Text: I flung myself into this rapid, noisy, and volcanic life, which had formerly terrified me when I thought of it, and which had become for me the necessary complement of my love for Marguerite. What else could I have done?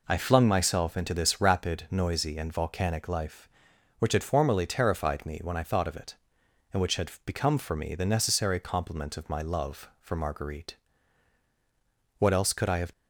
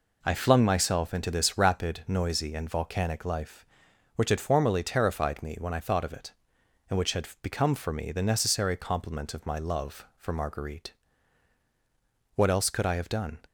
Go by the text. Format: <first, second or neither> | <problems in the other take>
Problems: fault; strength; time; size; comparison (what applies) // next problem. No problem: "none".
second | stops before "done"; at 12.9 s